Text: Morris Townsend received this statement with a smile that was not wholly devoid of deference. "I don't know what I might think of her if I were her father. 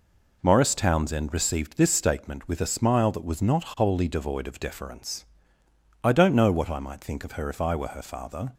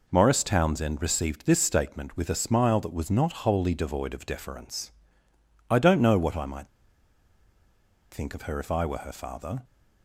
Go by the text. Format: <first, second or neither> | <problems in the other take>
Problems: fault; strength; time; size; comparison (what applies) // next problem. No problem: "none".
first | pauses between "might" and "think"; strong; at 6.6 s; 1.4 s long